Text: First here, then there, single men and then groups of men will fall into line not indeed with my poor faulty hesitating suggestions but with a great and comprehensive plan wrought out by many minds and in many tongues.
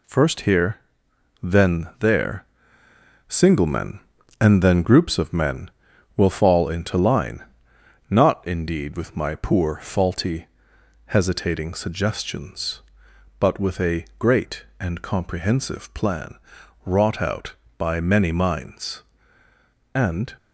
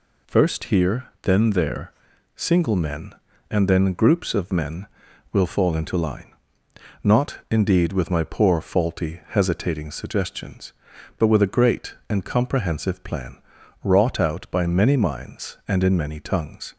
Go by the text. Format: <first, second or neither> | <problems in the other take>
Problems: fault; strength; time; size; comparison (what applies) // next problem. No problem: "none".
second | pauses between "line" and "not"; noticeable; at 7.4 s; 0.66 s long; noticeable in the second // pauses between "faulty" and "hesitating"; noticeable; at 10.4 s; 0.62 s long // pauses between "plan" and "wrought"; noticeable; at 16.3 s; 0.50 s long; noticeable in the second // stops before "in many tongues"; at 20.3 s